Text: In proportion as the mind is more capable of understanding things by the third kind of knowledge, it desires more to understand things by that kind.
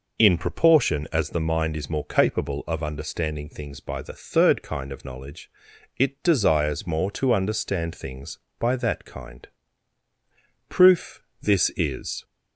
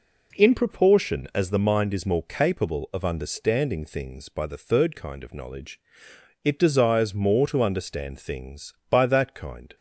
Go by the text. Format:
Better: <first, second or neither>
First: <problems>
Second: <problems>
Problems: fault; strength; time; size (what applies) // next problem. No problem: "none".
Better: second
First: goes on to say "Proof This is"; from 10.6 s on; 1.5 s long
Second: none